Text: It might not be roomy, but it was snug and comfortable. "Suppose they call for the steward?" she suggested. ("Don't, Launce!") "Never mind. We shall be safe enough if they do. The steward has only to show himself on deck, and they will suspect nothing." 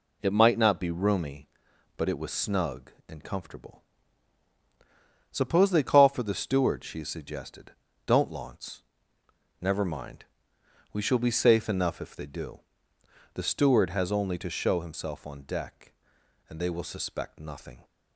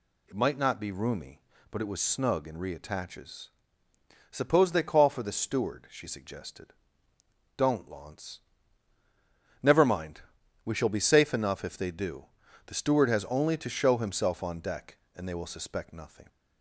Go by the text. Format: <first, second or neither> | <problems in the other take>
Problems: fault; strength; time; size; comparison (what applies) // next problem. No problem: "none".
first | says "reattaches" for "comfortable"; at 2.5 s